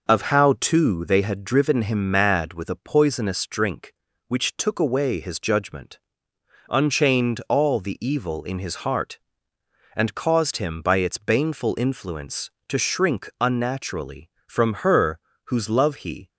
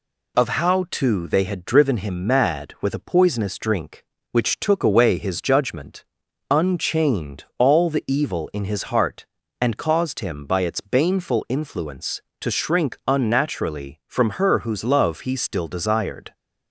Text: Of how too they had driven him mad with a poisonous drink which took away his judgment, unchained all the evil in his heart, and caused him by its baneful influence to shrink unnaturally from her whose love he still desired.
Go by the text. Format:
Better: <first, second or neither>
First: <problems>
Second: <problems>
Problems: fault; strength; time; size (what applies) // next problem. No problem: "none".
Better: second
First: pauses between "her" and "whose"; slight; at 15.1 s; 0.28 s long // stops before "still desired"; at 16.2 s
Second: none